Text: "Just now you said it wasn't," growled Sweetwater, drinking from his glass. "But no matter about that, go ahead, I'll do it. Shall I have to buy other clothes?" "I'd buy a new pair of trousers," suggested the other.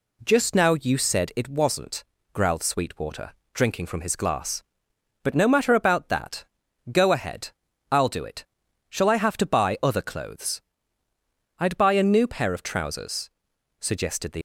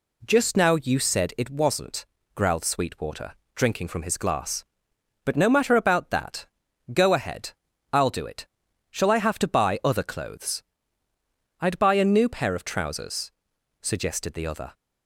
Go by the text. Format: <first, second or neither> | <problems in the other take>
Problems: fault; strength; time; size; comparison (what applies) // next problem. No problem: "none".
second | stops before "other"; at 14.3 s